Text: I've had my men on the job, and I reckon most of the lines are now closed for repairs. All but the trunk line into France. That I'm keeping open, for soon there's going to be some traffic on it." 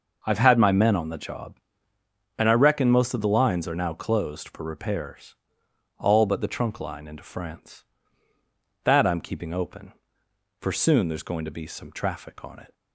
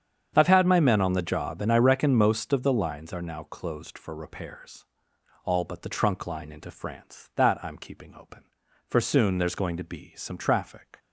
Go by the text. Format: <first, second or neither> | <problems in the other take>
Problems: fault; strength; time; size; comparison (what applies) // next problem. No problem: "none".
first | starts louder than the rest; strong; until 1.3 s; 8 dB // stops before "on it"; at 10.9 s